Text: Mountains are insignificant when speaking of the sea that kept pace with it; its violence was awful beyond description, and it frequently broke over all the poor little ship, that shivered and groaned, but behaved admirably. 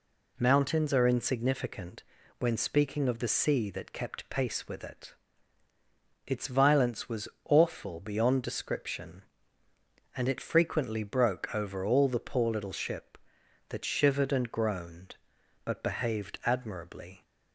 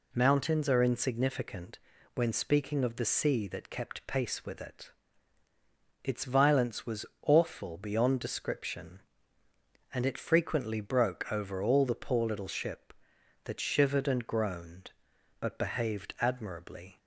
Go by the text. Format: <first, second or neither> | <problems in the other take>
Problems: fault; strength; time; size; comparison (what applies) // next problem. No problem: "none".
neither | pauses between "insignificant" and "when"; the same in both // pauses between "was" and "awful"; slight; the same in both